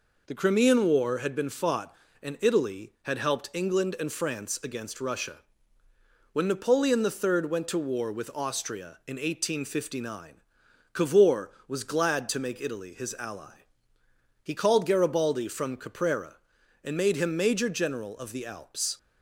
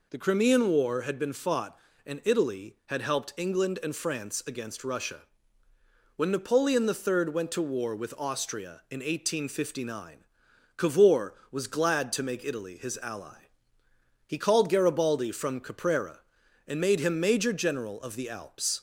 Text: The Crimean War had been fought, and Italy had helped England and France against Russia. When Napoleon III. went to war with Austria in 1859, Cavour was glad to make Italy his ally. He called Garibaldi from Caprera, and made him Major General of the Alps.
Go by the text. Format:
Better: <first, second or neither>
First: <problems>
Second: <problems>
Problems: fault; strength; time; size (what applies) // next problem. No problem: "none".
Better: second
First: gets quieter; slight; throughout; 3 dB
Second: none